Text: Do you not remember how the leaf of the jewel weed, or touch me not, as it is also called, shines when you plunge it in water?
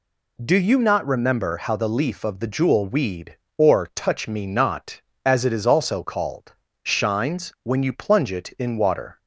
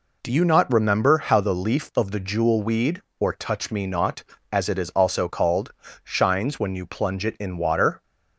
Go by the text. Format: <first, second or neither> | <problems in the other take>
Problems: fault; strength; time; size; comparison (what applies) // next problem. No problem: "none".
neither | none